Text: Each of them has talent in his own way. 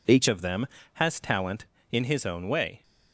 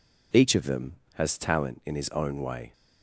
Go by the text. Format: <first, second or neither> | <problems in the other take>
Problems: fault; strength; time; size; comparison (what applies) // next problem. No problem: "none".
second | changes voice at "of"; from 0.2 s on; 2.6 s long